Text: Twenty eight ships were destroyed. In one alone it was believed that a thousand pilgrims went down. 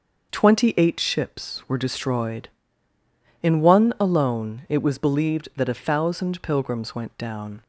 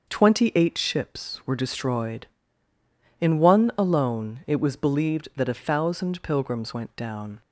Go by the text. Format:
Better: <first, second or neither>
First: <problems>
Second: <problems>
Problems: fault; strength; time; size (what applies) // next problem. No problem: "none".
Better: neither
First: starts louder than the rest; noticeable; until 1.3 s; 6 dB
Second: starts louder than the rest; until 1.1 s; 6 dB